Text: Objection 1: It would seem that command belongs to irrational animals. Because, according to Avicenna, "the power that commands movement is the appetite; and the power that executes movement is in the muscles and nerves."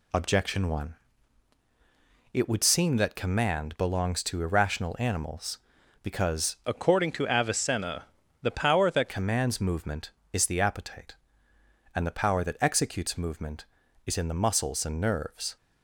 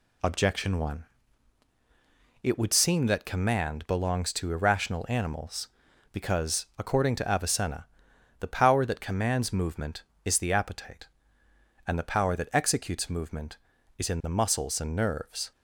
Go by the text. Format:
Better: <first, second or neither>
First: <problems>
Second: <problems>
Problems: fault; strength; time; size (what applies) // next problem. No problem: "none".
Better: second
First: changes voice from "according" to "that"; from 6.6 to 9.0 s; 2.4 s long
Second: none